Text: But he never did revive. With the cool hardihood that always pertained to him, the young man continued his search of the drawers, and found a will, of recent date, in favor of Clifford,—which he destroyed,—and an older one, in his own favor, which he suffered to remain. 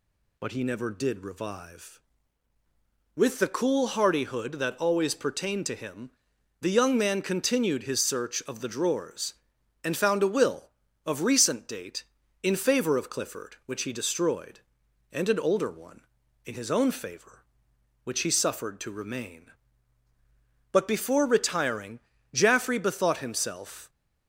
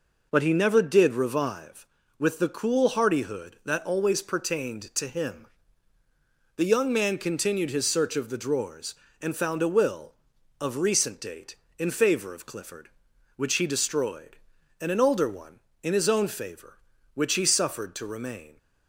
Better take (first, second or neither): second